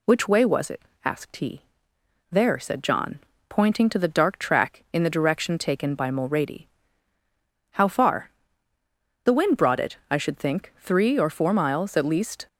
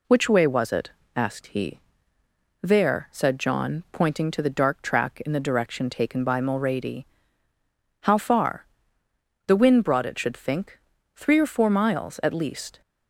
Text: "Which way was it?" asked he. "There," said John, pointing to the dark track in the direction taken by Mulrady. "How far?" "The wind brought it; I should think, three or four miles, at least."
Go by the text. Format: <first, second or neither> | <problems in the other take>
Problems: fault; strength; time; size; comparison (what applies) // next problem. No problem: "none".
first | skips "I"; at 10.1 s